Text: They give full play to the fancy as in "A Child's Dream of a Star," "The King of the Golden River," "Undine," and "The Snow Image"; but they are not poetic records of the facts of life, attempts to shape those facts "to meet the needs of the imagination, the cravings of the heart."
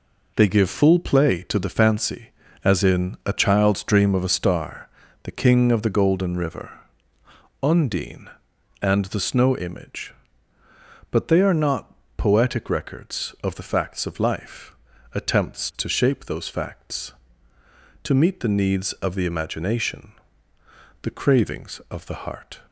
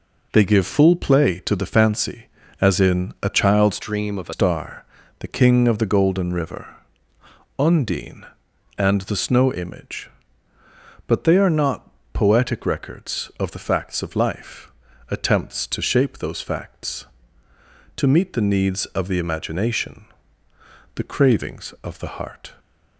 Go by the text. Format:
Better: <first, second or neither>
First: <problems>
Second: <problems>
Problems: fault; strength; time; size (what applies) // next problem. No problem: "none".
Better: first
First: pauses between "not" and "poetic"; slight; at 11.9 s; 0.24 s long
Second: changes voice from "Dream" to "a"; from 3.8 to 4.3 s; 0.5 s long // pauses between "not" and "poetic"; slight; at 11.8 s; 0.24 s long